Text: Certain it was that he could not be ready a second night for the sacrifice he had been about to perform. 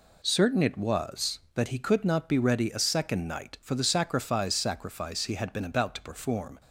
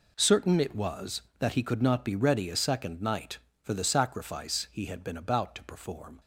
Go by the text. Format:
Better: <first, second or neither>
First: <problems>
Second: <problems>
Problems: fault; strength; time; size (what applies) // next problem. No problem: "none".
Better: second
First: says "sacrifice" twice; at 4.5 s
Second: none